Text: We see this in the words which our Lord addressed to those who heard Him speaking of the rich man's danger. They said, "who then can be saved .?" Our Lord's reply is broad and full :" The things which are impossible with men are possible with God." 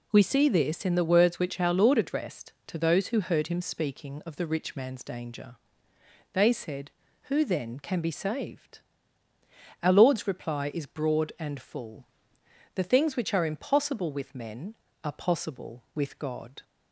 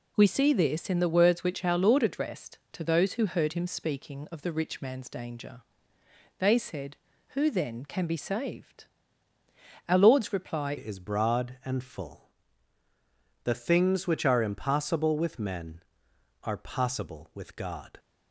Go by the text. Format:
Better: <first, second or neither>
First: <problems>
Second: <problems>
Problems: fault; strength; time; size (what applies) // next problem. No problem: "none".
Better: first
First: none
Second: changes voice at "is"; from 10.7 s on; 7.2 s long